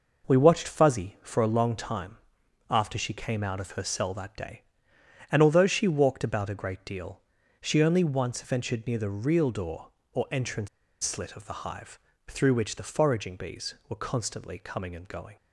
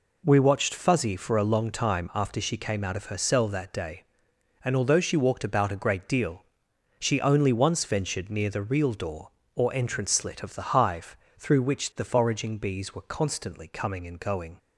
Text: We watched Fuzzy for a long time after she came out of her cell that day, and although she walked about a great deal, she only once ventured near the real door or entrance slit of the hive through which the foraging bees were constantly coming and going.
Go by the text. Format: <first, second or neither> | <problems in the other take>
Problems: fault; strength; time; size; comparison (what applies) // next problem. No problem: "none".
second | pauses between "time" and "after"; noticeable; at 2.1 s; 0.50 s long // pauses between "entrance" and "slit"; slight; at 10.6 s; 0.35 s long // pauses between "hive" and "through"; slight; at 12.0 s; 0.26 s long; slight in the second